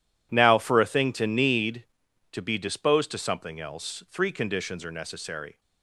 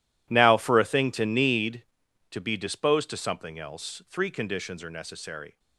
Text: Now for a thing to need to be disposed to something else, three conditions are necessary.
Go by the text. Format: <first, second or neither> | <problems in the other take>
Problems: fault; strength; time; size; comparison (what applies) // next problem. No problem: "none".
first | gets quieter; strong; throughout; 16.5 dB